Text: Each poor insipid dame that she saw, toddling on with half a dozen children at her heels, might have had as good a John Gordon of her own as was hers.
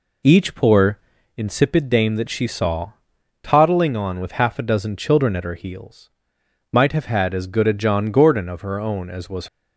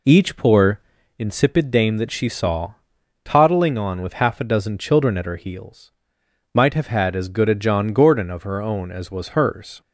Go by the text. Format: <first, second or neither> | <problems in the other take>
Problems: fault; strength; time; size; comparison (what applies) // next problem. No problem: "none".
second | pauses between "poor" and "insipid"; at 0.9 s; 0.38 s long; also in the second // stops before "hers"; at 9.4 s